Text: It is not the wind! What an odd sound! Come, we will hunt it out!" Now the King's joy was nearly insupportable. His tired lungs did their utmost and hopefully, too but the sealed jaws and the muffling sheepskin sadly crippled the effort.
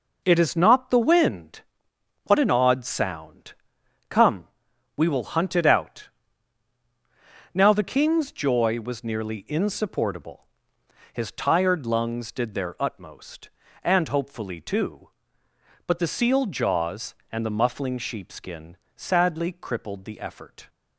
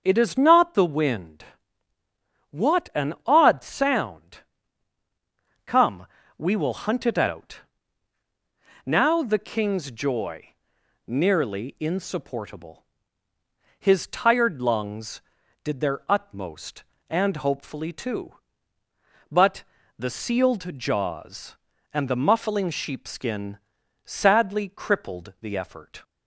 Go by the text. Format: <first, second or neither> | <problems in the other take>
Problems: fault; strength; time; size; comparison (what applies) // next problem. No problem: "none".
first | starts louder than the rest; until 1.0 s; 7 dB // skips "was"; at 10.7 s // pauses between "but" and "the"; slight; at 19.6 s; 0.36 s long // pauses between "sheepskin" and "sadly"; at 23.5 s; 0.44 s long; slight in the first